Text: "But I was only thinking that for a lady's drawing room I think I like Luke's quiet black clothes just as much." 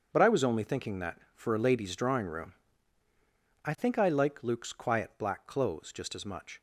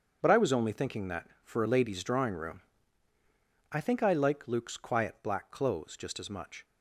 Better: neither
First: starts louder than the rest; until 1.1 s; 6.5 dB // pauses between "room" and "I"; at 2.5 s; 1.1 s long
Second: starts louder than the rest; until 1.2 s; 6.5 dB // pauses between "room" and "I"; at 2.6 s; 1.1 s long

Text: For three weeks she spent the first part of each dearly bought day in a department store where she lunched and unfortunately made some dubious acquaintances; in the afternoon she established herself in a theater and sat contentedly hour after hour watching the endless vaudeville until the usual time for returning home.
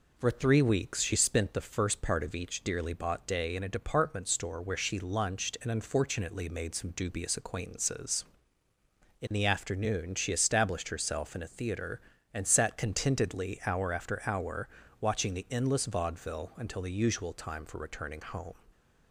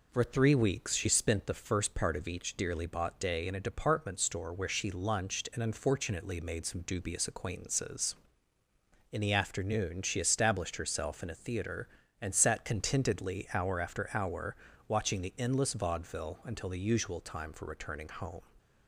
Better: neither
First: pauses between "hour" and "watching"; slight; at 14.6 s; 0.32 s long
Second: pauses between "hour" and "watching"; slight; at 14.5 s; 0.32 s long

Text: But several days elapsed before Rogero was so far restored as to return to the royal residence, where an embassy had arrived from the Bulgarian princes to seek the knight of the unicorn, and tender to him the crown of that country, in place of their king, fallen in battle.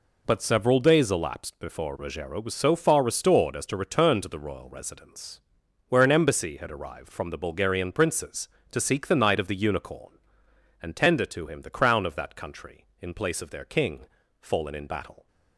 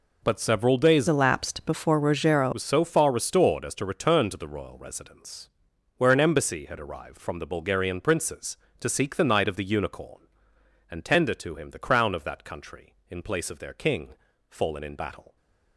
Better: first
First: none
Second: changes voice from "elapsed" to "Rogero"; from 1.0 to 2.5 s; 1.5 s long

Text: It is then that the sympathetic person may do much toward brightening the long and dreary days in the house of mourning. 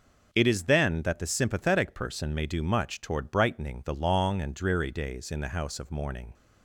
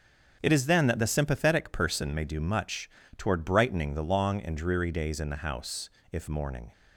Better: first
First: none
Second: starts louder than the rest; until 1.4 s; 7 dB // pauses between "much" and "toward"; slight; at 2.8 s; 0.28 s long // says "if" for "of"; at 6.1 s

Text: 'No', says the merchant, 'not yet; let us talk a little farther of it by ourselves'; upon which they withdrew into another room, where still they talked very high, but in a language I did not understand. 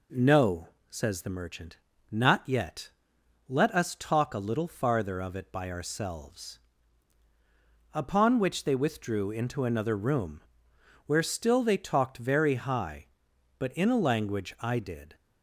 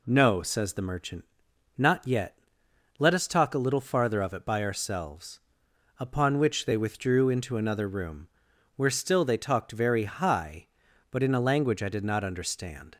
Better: second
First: stops before "not understand"; at 15.1 s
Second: none

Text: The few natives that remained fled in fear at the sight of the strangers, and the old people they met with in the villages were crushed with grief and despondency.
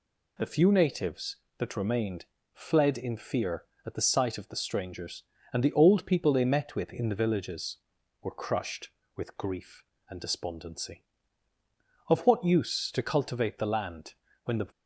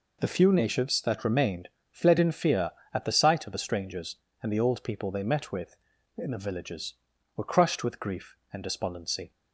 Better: second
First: pauses between "remained" and "fled"; slight; at 2.2 s; 0.26 s long // goes on to say "Of what use to cultivate the land when the"; strong; from 12.0 s on; 2.6 s long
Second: pauses between "remained" and "fled"; slight; at 1.6 s; 0.22 s long

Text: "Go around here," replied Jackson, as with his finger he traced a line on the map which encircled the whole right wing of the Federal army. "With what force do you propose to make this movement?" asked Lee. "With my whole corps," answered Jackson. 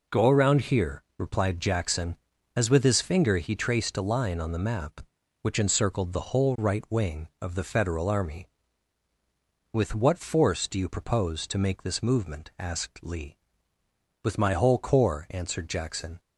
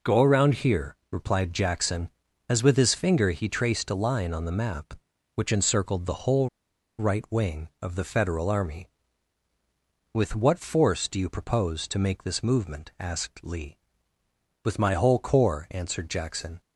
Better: first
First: none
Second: pauses between "whole" and "right"; noticeable; at 6.4 s; 0.50 s long

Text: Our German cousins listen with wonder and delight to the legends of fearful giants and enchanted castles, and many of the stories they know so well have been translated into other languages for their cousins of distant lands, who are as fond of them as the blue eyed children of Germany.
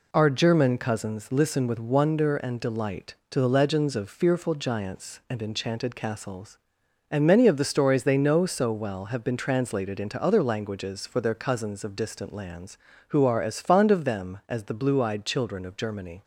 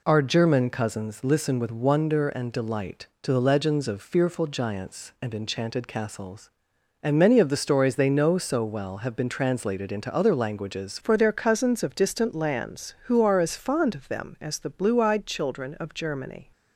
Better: first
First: none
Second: changes voice at "for"; from 11.0 s on; 5.5 s long

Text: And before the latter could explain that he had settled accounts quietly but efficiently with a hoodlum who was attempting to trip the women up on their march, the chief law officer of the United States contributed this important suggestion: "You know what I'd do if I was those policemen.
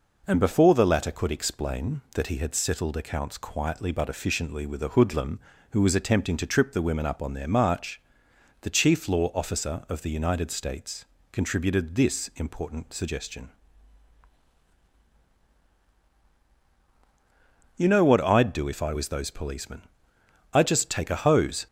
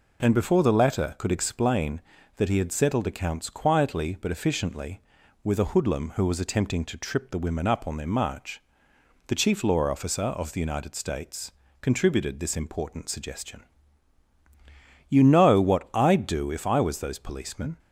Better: second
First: pauses between "States" and "contributed"; slight; at 11.0 s; 0.28 s long // goes on to say "I'd just take a hose"; noticeable; from 20.5 s on; 1.1 s long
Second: pauses between "States" and "contributed"; slight; at 11.5 s; 0.30 s long

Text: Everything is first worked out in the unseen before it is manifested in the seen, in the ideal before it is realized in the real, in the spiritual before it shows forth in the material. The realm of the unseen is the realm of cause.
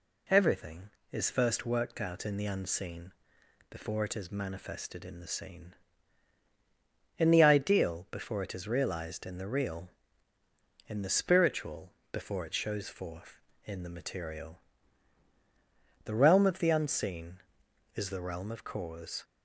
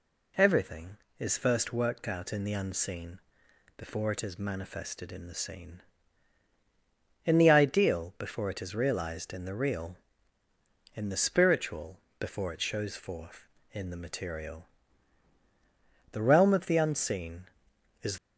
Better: first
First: pauses between "unseen" and "before"; noticeable; at 3.1 s; 0.58 s long // pauses between "spiritual" and "before"; slight; at 11.9 s; 0.20 s long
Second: pauses between "unseen" and "before"; noticeable; at 3.1 s; 0.58 s long // pauses between "spiritual" and "before"; slight; at 11.9 s; 0.20 s long // stops before "the realm of cause"; at 18.1 s

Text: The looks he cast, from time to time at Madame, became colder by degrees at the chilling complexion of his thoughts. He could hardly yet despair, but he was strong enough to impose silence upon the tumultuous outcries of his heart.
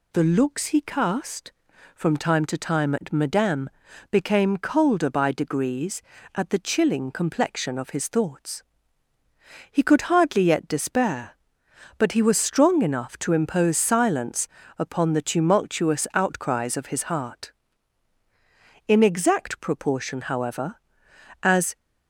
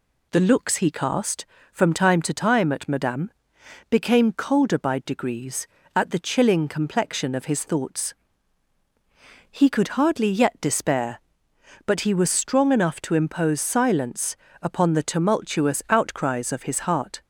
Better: second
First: pauses between "silence" and "upon"; slight; at 14.4 s; 0.30 s long // goes on to say "In exact proportion however as"; strong; from 18.8 s on; 2.8 s long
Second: pauses between "silence" and "upon"; slight; at 14.3 s; 0.28 s long

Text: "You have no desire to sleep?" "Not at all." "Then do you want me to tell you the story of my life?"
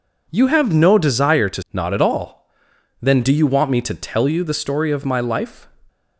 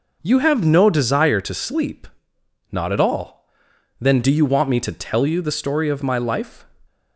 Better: second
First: skips "sleep"; at 1.6 s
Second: none

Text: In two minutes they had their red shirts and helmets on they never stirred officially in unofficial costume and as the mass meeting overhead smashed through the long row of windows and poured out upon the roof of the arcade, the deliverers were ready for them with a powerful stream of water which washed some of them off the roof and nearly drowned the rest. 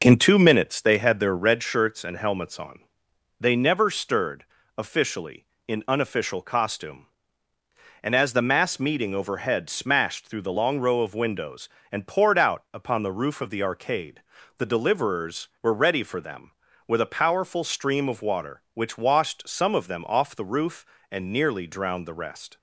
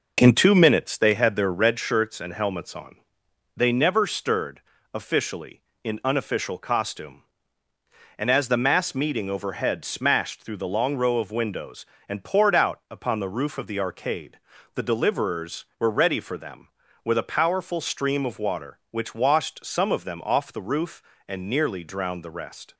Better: neither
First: pauses between "on" and "they"; noticeable; at 2.8 s; 0.58 s long // pauses between "stirred" and "officially"; slight; at 4.4 s; 0.32 s long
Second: pauses between "on" and "they"; noticeable; at 2.9 s; 0.58 s long // pauses between "stirred" and "officially"; slight; at 4.6 s; 0.32 s long

